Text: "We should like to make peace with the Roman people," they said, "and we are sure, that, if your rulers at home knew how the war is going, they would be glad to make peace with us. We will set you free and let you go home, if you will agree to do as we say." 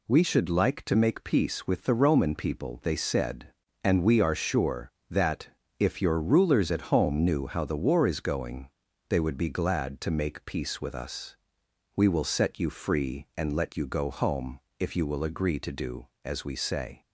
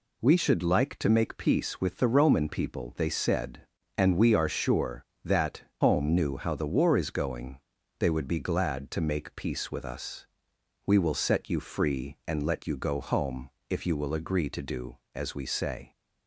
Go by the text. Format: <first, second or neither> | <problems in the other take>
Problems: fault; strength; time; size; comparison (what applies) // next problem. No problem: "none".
first | skips "if your rulers at"; at 5.7 s